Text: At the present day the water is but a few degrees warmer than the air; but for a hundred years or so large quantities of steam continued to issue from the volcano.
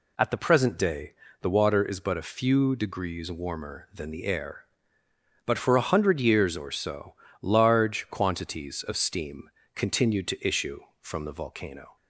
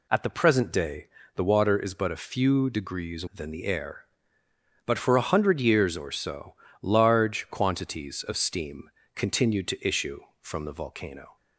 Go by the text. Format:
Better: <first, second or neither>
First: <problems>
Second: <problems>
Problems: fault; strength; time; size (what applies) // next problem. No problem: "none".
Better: first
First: pauses between "day" and "the"; slight; at 1.1 s; 0.28 s long // pauses between "so" and "large"; slight; at 7.1 s; 0.28 s long // pauses between "steam" and "continued"; slight; at 9.4 s; 0.24 s long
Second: pauses between "day" and "the"; slight; at 1.0 s; 0.28 s long // skips "warmer"; at 3.2 s // pauses between "so" and "large"; slight; at 6.5 s; 0.28 s long // pauses between "steam" and "continued"; slight; at 8.8 s; 0.24 s long